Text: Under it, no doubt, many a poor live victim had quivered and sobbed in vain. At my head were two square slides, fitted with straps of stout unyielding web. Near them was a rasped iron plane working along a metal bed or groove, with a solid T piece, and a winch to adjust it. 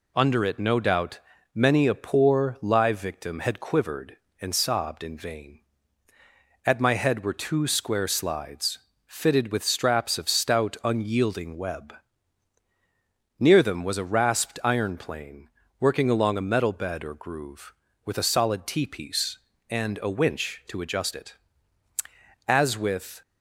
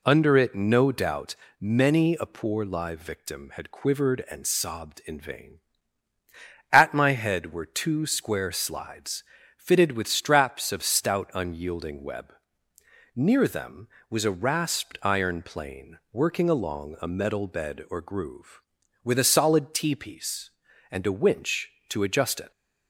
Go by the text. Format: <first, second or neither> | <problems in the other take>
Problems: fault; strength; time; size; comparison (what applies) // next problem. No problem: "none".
second | pauses between "plane" and "working"; slight; at 15.4 s; 0.32 s long // goes on to say "As with"; noticeable; from 22.4 s on; 0.74 s long